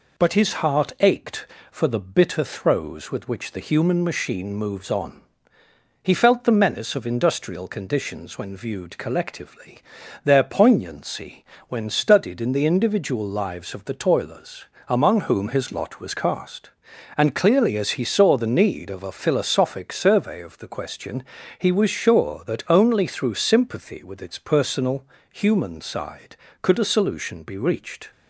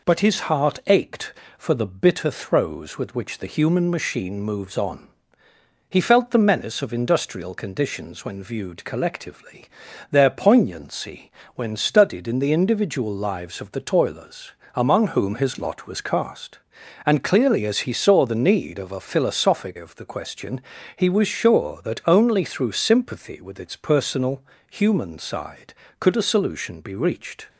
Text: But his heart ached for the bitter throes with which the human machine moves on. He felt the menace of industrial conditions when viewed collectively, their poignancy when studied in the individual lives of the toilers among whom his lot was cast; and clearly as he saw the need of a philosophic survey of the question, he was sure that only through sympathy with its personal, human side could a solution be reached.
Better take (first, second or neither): first